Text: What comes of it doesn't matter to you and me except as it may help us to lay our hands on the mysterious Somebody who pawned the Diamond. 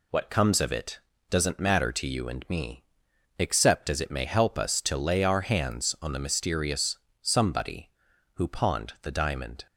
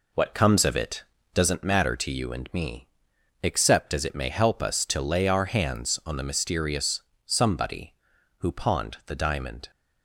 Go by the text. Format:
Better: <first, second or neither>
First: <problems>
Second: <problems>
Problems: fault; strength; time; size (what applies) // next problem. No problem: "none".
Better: first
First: pauses between "it" and "doesn't"; slight; at 1.0 s; 0.30 s long // pauses between "me" and "except"; noticeable; at 2.8 s; 0.56 s long // pauses between "mysterious" and "Somebody"; slight; at 6.9 s; 0.24 s long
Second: starts louder than the rest; until 1.6 s; 3.5 dB // pauses between "it" and "doesn't"; slight; at 1.0 s; 0.30 s long // pauses between "me" and "except"; noticeable; at 2.8 s; 0.56 s long // pauses between "mysterious" and "Somebody"; slight; at 7.0 s; 0.24 s long